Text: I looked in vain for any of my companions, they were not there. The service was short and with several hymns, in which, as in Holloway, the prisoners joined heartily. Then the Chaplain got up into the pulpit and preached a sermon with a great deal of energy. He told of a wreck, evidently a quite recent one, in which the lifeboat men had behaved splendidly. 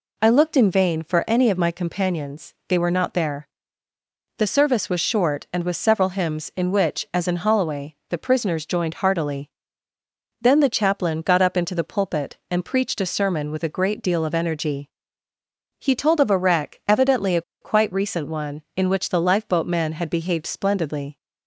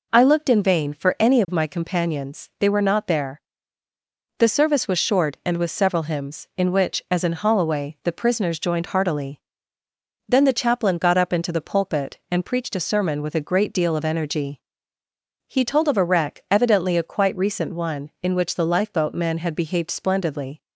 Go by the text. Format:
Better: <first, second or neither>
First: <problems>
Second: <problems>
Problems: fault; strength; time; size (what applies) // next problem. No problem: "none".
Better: second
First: pauses between "a" and "quite"; slight; at 17.4 s; 0.20 s long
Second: none